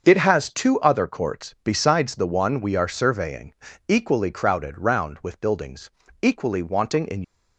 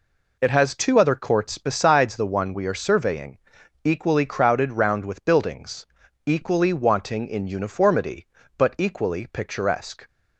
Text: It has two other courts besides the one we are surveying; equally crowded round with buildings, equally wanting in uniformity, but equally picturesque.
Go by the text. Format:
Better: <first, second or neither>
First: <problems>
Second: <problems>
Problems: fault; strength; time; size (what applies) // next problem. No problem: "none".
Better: second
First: starts louder than the rest; until 1.0 s; 6.5 dB // stops before "uniformity but equally picturesque"; at 7.2 s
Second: none